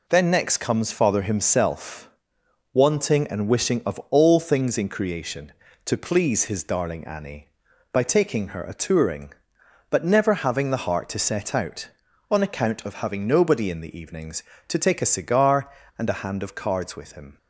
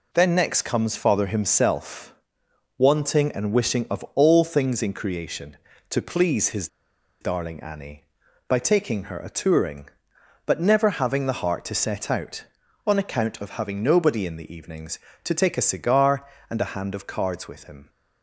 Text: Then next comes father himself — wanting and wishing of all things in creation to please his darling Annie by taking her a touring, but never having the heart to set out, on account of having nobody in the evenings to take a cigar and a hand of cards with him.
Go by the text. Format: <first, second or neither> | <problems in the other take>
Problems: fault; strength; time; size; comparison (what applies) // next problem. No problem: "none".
first | pauses between "his" and "darling"; noticeable; at 6.6 s; 0.53 s long